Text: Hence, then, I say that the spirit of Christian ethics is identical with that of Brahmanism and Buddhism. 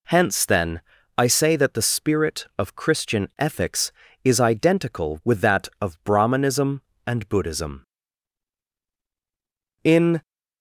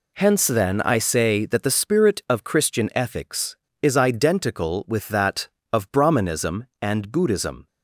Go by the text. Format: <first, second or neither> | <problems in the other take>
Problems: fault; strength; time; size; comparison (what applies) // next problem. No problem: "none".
second | goes on to say "In"; slight; from 9.8 s on; 0.38 s long